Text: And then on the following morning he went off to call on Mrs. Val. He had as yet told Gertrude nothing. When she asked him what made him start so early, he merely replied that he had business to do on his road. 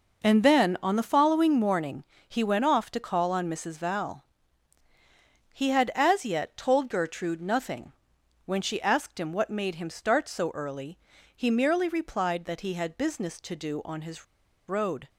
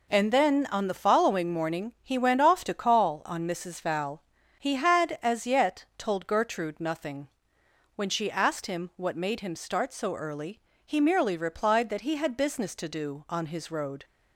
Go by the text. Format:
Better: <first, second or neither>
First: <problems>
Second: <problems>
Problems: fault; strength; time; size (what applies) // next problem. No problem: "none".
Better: second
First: pauses between "morning" and "he"; slight; at 2.0 s; 0.24 s long // pauses between "his" and "road"; at 14.2 s; 0.43 s long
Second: none